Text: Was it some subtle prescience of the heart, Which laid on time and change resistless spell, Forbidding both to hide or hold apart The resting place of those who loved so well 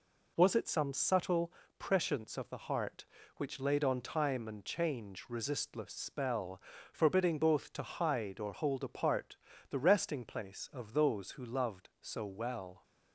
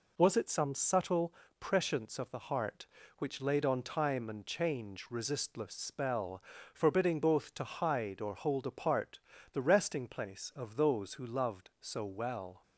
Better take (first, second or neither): neither